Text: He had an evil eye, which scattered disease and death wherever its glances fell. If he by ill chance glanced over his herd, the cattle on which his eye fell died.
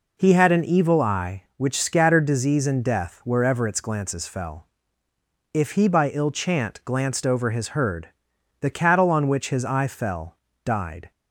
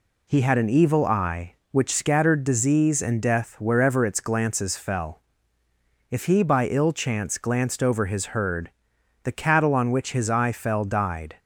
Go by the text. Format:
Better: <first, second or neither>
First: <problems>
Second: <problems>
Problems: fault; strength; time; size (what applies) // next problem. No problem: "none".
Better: second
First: says "chant" for "chance"; at 6.3 s // pauses between "fell" and "died"; slight; at 10.3 s; 0.30 s long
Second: none